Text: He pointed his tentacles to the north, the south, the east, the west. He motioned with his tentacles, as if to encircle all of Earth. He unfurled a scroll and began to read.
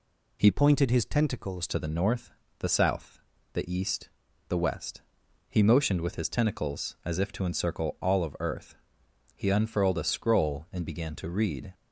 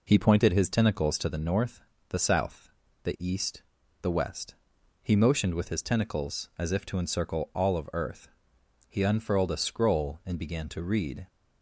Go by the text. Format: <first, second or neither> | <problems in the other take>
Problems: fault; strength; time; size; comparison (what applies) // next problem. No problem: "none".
second | changes voice from "pointed" to "tentacles"; from 0.5 to 1.6 s; 1.1 s long